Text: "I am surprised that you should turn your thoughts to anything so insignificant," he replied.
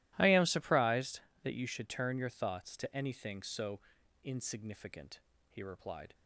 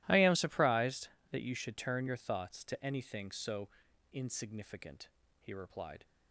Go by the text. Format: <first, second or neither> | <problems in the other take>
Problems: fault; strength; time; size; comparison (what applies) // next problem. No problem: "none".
neither | starts louder than the rest; strong; the same in both // pauses between "so" and "insignificant"; the same in both